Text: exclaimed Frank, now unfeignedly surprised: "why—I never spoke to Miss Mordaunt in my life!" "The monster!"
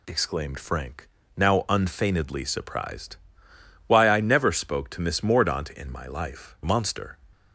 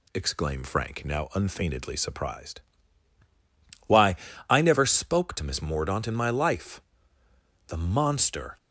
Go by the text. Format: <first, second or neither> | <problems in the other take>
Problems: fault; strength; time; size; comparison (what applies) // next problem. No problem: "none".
second | skips "The"; at 6.6 s